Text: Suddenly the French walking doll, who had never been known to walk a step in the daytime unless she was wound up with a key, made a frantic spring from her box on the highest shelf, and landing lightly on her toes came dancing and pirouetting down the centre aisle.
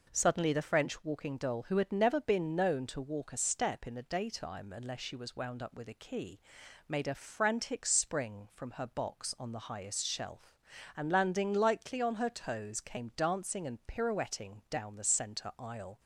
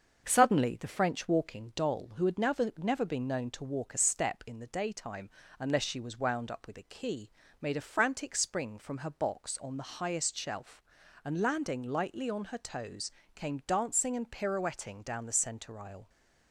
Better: first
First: none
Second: starts louder than the rest; until 1.3 s; 6.5 dB // says "never" twice; at 2.7 s // pauses between "daytime" and "unless"; slight; at 5.2 s; 0.30 s long // pauses between "toes" and "came"; slight; at 13.1 s; 0.24 s long

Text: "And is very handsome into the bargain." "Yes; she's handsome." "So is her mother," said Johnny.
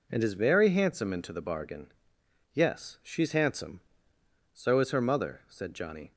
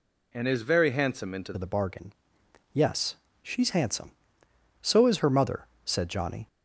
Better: first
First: none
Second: changes voice at "the"; from 1.5 s on; 4.9 s long

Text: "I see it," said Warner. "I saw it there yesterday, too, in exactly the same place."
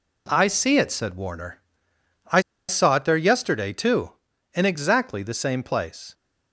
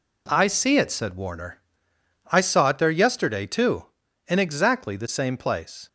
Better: second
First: pauses between "I" and "saw"; slight; at 2.4 s; 0.27 s long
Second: none

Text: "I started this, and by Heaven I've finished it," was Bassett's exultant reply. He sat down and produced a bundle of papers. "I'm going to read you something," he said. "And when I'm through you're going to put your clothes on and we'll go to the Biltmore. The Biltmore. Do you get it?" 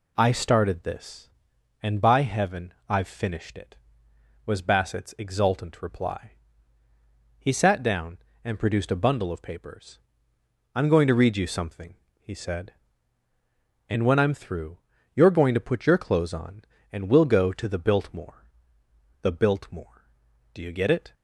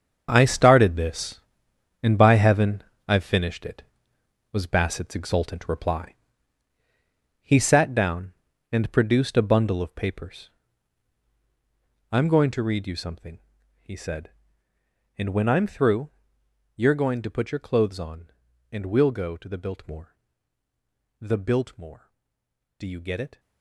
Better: first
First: pauses between "through" and "you're"; at 14.7 s; 0.38 s long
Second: gets quieter; strong; throughout; 13 dB // pauses between "Heaven" and "I've"; slight; at 2.8 s; 0.24 s long // pauses between "through" and "you're"; noticeable; at 16.0 s; 0.66 s long

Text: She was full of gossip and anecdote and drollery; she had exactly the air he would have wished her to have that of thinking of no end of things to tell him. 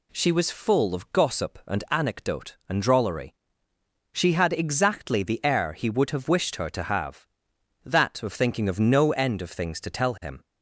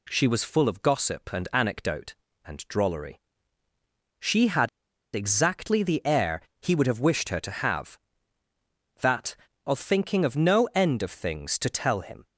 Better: first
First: none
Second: pauses between "had" and "exactly"; noticeable; at 4.6 s; 0.47 s long // pauses between "air" and "he"; slight; at 6.4 s; 0.18 s long

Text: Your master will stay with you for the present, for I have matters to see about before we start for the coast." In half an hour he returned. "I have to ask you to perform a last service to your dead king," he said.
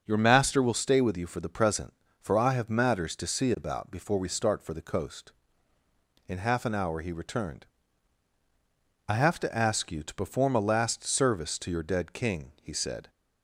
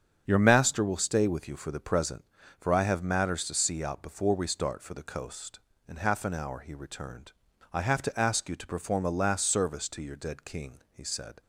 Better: first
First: starts louder than the rest; until 1.0 s; 6.5 dB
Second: starts louder than the rest; strong; until 1.2 s; 7.5 dB // says "out" for "about"; at 3.8 s

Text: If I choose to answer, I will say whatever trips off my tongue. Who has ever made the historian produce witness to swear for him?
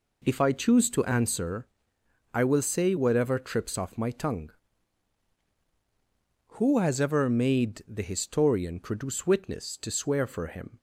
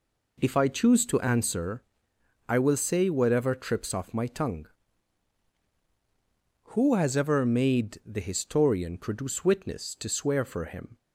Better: neither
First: none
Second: none

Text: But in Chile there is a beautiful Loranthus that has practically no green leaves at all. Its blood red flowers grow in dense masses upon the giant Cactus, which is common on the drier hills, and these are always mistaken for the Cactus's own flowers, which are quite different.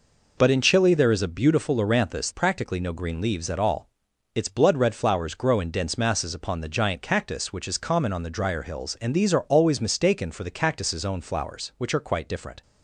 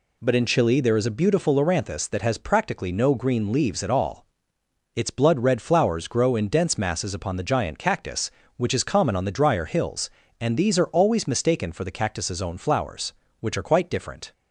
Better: second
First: skips "that has"; at 2.3 s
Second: none

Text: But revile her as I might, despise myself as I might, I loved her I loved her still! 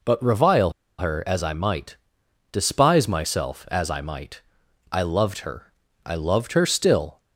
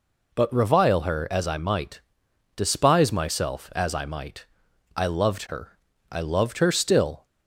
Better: second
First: pauses between "revile" and "her"; slight; at 0.7 s; 0.26 s long // pauses between "her" and "I"; slight; at 5.7 s; 0.32 s long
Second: pauses between "her" and "I"; slight; at 5.7 s; 0.32 s long

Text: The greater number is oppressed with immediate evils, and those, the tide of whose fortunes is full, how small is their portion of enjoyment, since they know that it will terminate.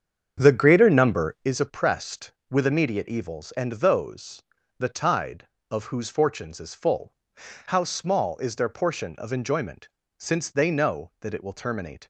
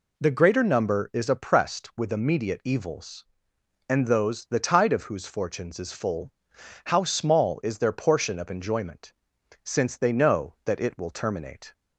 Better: second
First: starts louder than the rest; strong; until 1.5 s; 7.5 dB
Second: none

